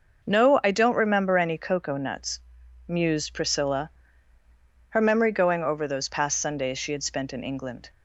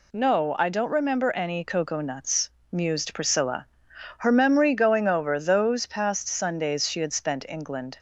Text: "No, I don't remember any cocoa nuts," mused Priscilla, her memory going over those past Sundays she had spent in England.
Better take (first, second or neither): first